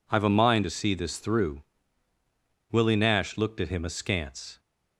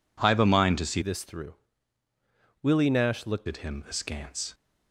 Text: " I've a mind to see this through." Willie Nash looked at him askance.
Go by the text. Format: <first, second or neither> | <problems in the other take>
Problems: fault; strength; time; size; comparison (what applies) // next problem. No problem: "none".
first | changes voice from "this" to "looked"; from 1.0 to 3.4 s; 2.4 s long